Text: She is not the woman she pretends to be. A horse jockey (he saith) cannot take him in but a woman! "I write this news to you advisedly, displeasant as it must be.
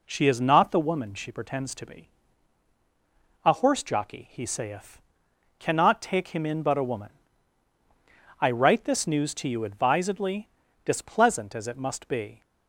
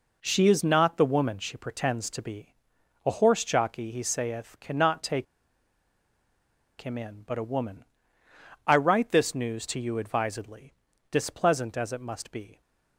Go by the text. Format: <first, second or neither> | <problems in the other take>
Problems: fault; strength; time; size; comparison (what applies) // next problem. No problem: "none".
first | pauses between "take" and "him"; strong; at 5.2 s; 1.5 s long